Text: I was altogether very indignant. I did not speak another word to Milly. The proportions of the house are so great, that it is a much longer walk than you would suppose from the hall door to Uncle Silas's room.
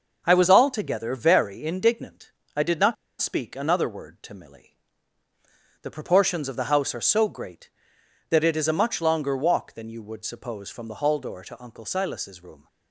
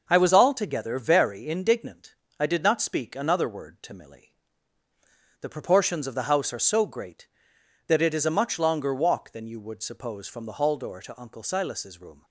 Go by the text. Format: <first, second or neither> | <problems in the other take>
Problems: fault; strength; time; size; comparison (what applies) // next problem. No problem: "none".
second | starts louder than the rest; noticeable; until 1.2 s; 6 dB; noticeable in the second // pauses between "not" and "speak"; slight; at 2.9 s; 0.25 s long